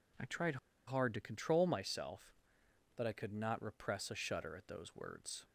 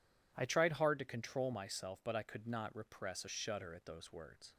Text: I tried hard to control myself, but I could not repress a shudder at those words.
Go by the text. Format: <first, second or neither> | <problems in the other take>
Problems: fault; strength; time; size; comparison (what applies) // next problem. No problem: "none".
second | pauses between "tried" and "hard"; slight; at 0.5 s; 0.30 s long